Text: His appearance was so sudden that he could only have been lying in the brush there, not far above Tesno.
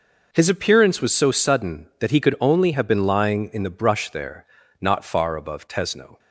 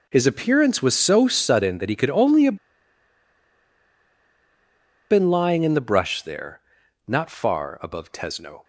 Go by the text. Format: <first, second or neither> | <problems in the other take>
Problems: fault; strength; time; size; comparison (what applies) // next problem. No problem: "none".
first | pauses between "have" and "been"; strong; at 2.5 s; 2.5 s long